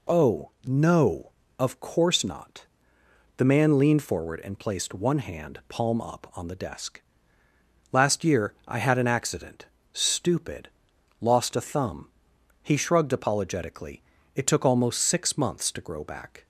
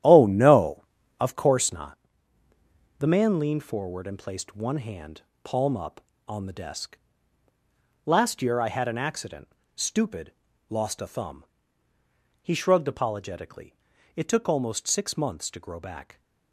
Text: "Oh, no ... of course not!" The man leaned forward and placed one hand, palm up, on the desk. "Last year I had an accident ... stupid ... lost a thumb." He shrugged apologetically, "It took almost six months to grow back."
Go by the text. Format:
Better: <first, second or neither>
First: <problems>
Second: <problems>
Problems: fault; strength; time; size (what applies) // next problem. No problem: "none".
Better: first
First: none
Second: starts louder than the rest; strong; until 1.5 s; 11.5 dB